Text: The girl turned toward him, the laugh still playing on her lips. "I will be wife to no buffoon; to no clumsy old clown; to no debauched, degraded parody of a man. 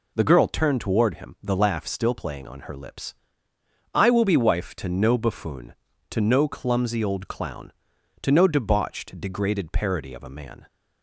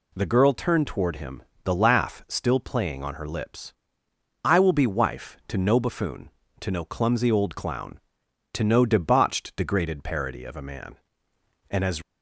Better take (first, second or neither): first